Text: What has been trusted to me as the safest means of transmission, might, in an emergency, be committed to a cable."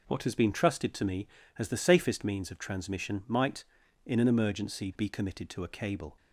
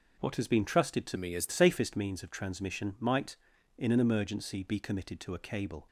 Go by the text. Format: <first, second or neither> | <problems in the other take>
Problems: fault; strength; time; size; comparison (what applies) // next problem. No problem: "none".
first | changes voice from "me" to "the"; from 1.1 to 1.5 s; 0.4 s long